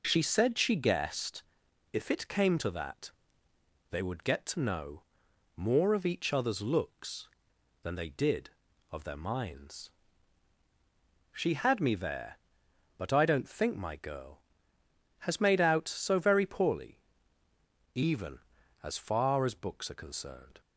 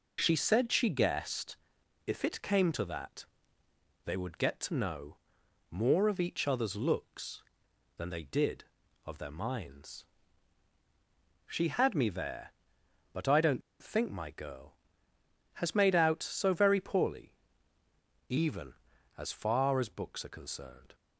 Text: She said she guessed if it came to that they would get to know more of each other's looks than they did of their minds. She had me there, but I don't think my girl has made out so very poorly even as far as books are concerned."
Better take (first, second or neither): first